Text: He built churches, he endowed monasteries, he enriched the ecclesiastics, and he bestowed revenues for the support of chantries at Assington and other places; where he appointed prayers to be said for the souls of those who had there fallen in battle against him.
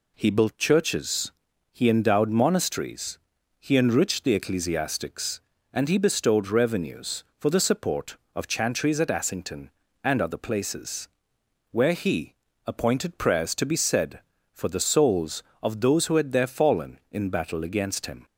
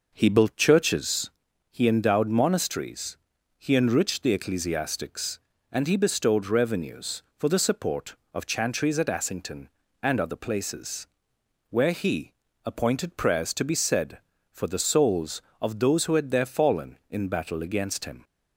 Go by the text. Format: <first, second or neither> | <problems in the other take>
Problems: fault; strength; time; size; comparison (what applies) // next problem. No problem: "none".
first | starts louder than the rest; noticeable; until 1.2 s; 5.5 dB // pauses between "he" and "appointed"; slight; at 12.3 s; 0.32 s long; slight in the first